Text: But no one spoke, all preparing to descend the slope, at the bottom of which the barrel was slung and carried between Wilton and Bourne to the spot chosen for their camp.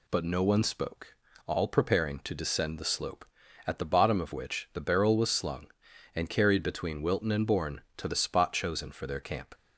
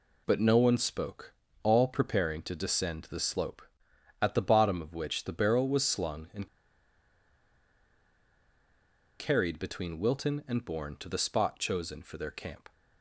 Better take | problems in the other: first | pauses between "and" and "carried"; strong; at 6.4 s; 2.7 s long

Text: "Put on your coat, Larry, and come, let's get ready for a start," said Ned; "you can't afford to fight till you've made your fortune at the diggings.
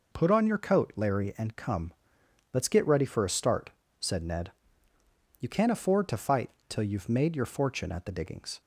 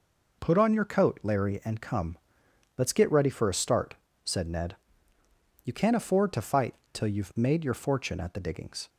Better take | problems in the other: neither | pauses between "fight" and "till"; slight; the same in both

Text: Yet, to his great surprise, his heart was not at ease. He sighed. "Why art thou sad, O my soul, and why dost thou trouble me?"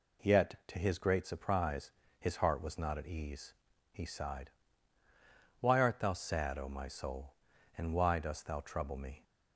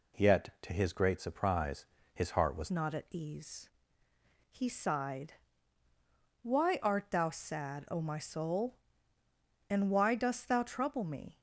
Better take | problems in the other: first | changes voice at "not"; from 2.6 s on; 8.7 s long

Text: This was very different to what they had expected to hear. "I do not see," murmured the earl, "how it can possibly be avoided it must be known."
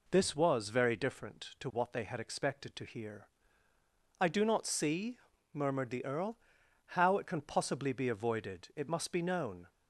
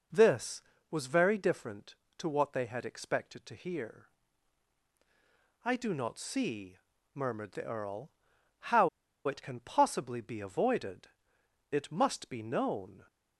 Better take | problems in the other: first | pauses between "how" and "it"; at 8.8 s; 0.37 s long // pauses between "avoided" and "it"; noticeable; at 11.0 s; 0.64 s long

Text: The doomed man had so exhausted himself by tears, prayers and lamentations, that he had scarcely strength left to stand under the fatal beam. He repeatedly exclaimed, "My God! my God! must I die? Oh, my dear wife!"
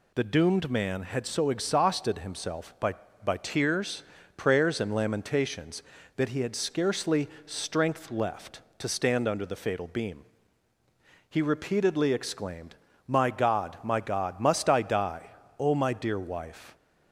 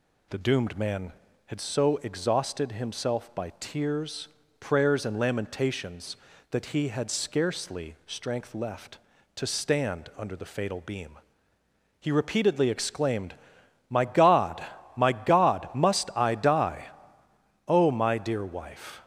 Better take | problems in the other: second | says "by" twice; at 3.2 s // pauses between "scarcely" and "strength"; slight; at 7.2 s; 0.18 s long

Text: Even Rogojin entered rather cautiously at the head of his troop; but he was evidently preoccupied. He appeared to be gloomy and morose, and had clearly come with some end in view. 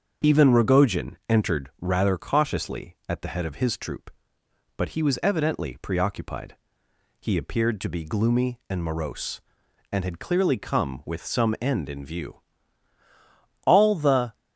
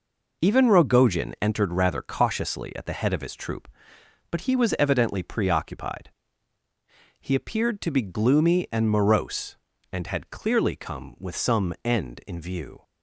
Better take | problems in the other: second | starts louder than the rest; until 1.3 s; 6.5 dB // goes on to say "All the"; noticeable; from 13.6 s on; 0.70 s long

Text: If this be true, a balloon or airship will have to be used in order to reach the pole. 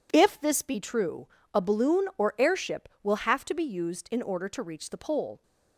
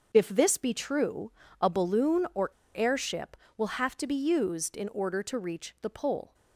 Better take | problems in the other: first | starts louder than the rest; until 1.1 s; 6.5 dB // pauses between "or" and "airship"; slight; at 2.4 s; 0.25 s long

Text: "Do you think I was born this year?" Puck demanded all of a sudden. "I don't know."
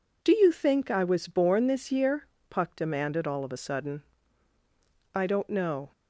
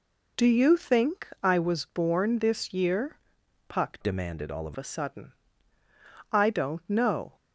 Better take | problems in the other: first | pauses between "think" and "I"; slight; at 1.2 s; 0.16 s long // changes voice from "demanded" to "of"; from 4.0 to 4.7 s; 0.7 s long

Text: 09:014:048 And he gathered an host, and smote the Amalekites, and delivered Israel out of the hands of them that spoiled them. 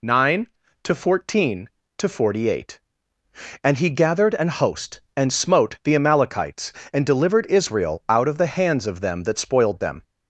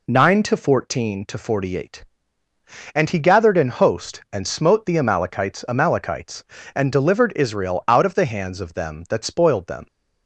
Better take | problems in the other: first | says "Amalekites" twice; at 5.6 s

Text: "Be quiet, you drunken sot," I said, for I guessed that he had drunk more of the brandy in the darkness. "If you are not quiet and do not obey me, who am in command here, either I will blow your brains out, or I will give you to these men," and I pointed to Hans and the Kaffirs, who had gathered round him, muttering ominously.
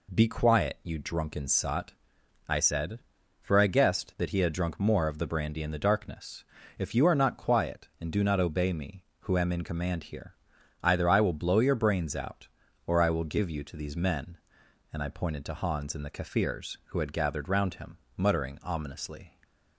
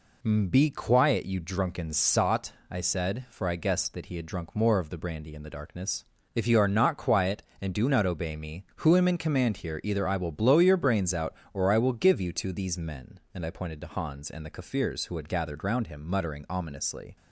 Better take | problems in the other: neither | none

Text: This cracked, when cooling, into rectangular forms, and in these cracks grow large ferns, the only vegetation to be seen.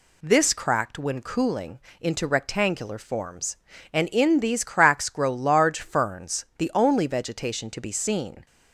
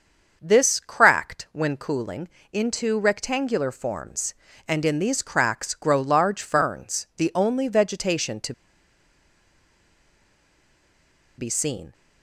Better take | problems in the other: first | starts louder than the rest; until 1.4 s; 6.5 dB // pauses between "to" and "be"; strong; at 8.5 s; 2.8 s long

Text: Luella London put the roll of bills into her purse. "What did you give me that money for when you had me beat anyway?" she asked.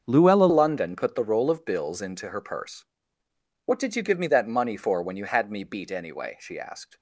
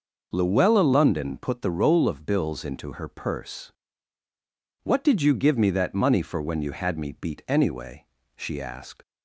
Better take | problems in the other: second | starts louder than the rest; until 1.0 s; 6.5 dB // changes voice at "London"; from 0.4 s on; 6.5 s long

